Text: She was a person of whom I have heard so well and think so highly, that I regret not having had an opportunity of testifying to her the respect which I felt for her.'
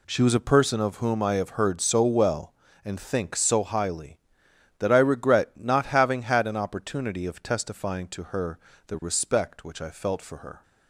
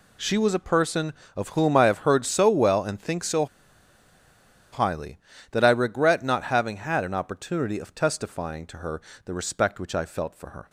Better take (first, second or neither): first